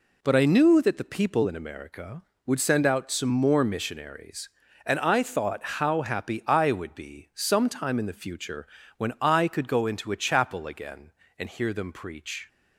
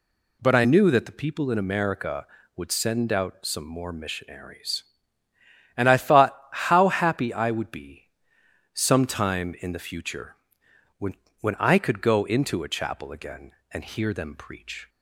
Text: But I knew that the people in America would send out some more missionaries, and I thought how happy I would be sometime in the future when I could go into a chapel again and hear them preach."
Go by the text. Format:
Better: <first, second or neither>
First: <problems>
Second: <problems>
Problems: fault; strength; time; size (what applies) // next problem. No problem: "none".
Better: first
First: pauses between "future" and "when"; slight; at 8.6 s; 0.32 s long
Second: pauses between "be" and "sometime"; noticeable; at 8.0 s; 0.68 s long // pauses between "future" and "when"; noticeable; at 10.3 s; 0.64 s long // says "when" twice; at 11.4 s